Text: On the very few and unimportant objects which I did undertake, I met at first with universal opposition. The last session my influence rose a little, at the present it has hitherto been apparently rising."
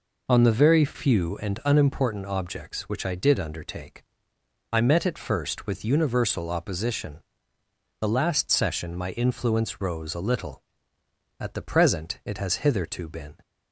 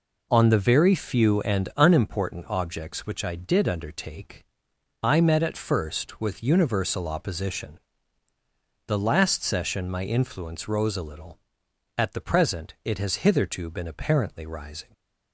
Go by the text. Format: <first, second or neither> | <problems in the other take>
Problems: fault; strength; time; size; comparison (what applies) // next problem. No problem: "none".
second | stops before "apparently rising"; at 13.4 s